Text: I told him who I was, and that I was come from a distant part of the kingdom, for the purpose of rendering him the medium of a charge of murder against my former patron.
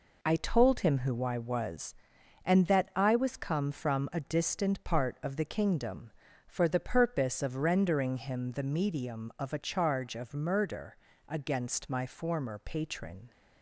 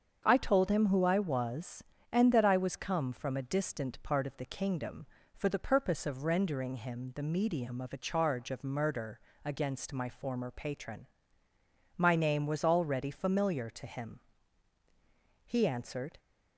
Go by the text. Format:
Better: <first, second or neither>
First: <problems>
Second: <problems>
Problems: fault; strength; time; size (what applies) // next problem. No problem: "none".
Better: first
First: pauses between "murder" and "against"; slight; at 10.9 s; 0.32 s long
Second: starts louder than the rest; until 1.2 s; 7 dB // pauses between "murder" and "against"; slight; at 9.1 s; 0.24 s long // goes on to say "My name was already familiar to him He answered"; strong; from 11.9 s on; 4.2 s long